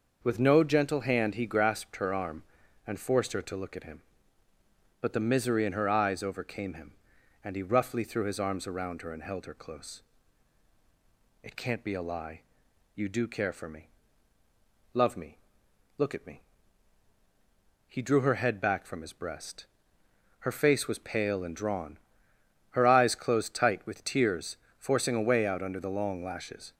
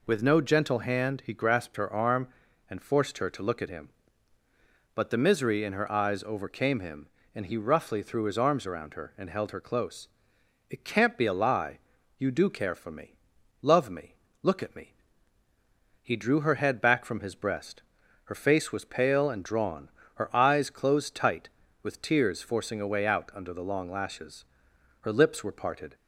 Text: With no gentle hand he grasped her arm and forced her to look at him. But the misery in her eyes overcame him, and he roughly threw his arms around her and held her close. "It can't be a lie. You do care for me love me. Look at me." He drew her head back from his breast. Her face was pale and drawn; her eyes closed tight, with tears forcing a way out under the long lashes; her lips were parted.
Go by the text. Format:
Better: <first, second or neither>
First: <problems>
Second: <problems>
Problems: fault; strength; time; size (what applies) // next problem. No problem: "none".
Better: second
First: starts louder than the rest; noticeable; until 1.2 s; 6 dB // pauses between "me" and "love"; at 13.8 s; 1.0 s long // pauses between "tears" and "forcing"; slight; at 24.5 s; 0.20 s long // stops before "her lips were parted"; at 26.7 s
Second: pauses between "me" and "love"; noticeable; at 13.1 s; 0.46 s long